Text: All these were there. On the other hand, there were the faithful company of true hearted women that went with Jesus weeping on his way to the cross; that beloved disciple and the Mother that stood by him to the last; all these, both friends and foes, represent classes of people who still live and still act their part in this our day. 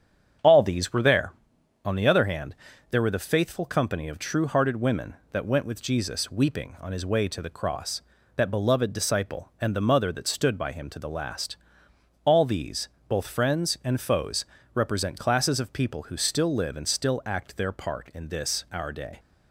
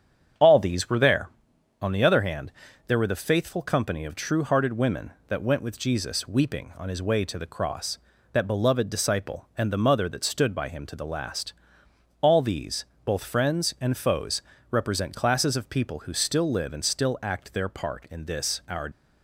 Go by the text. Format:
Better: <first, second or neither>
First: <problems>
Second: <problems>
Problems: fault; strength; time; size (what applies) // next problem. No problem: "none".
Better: first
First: starts louder than the rest; strong; until 1.9 s; 8.5 dB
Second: starts louder than the rest; strong; until 1.8 s; 8.5 dB // stops before "day"; at 18.9 s